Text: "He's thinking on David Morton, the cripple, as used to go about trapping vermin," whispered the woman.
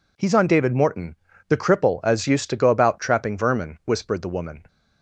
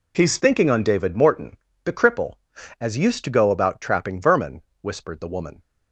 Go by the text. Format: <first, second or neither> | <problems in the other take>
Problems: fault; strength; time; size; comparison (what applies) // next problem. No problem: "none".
second | skips "thinking"; at 0.3 s